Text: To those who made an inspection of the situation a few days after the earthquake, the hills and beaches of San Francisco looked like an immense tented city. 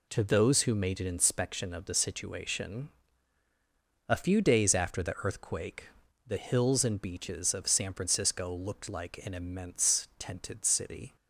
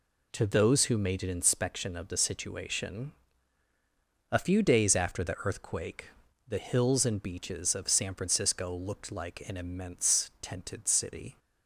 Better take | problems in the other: neither | pauses between "situation" and "a"; the same in both

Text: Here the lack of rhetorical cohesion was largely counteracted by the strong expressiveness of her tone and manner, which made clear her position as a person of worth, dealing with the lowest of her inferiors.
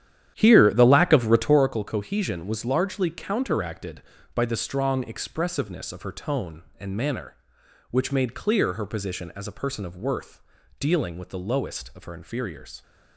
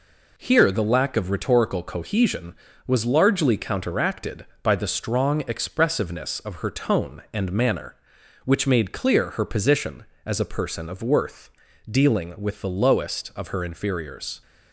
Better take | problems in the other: second | starts louder than the rest; strong; until 1.8 s; 10.5 dB

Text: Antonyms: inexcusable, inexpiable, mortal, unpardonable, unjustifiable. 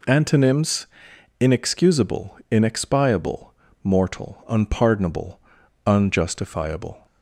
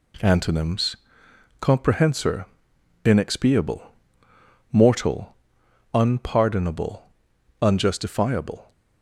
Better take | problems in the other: first | says "comprehensor" for "inexcusable"; at 1.5 s

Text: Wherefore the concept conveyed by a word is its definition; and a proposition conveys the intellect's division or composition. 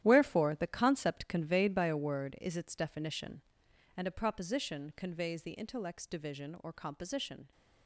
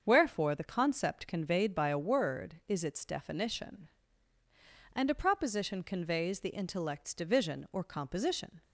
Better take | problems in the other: second | gets quieter; strong; throughout; 12 dB // starts louder than the rest; strong; until 1.0 s; 11.5 dB; also in the second

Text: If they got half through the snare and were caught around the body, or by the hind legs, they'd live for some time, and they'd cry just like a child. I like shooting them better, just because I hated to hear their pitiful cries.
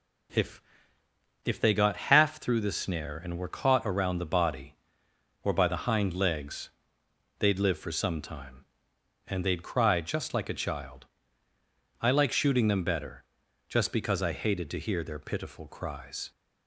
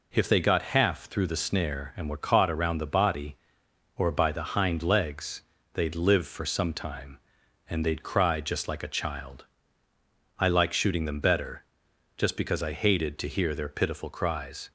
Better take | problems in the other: second | says "If" twice; at 1.4 s

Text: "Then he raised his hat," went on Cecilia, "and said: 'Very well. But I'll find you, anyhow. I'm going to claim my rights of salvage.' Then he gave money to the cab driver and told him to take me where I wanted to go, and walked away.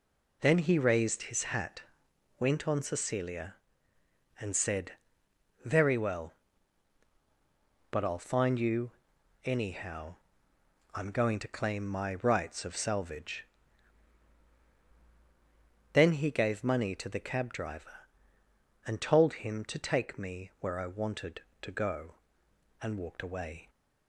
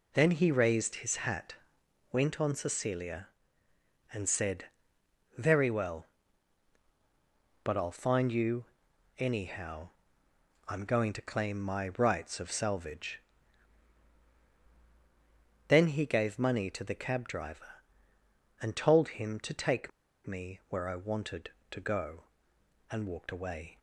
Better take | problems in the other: first | pauses between "take" and "me"; at 19.9 s; 0.36 s long

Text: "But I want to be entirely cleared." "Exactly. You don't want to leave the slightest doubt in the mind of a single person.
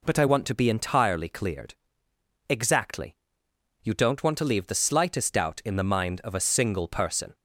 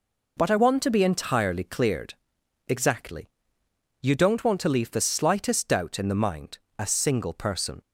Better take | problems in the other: first | skips "of"; at 6.6 s

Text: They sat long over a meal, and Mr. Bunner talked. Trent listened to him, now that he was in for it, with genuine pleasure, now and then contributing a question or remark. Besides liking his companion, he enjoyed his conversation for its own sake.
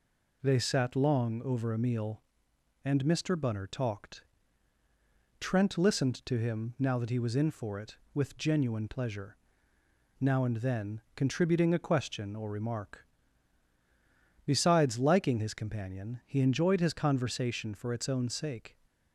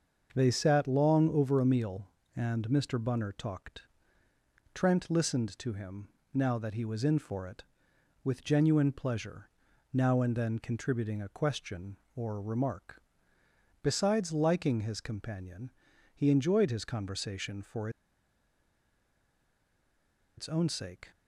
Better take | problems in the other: first | starts louder than the rest; until 1.3 s; 6.5 dB // pauses between "for" and "its"; strong; at 17.8 s; 2.4 s long

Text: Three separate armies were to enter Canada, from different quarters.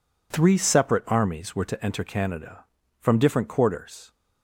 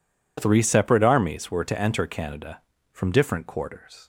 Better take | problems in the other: neither | none

